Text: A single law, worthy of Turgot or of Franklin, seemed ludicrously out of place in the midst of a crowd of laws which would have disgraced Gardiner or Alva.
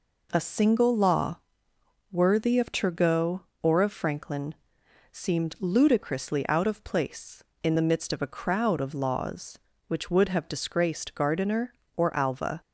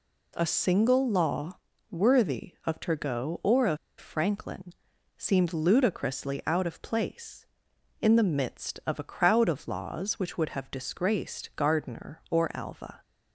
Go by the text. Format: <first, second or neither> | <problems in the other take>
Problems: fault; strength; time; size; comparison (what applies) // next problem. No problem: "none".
first | pauses between "of" and "Franklin"; slight; at 3.7 s; 0.21 s long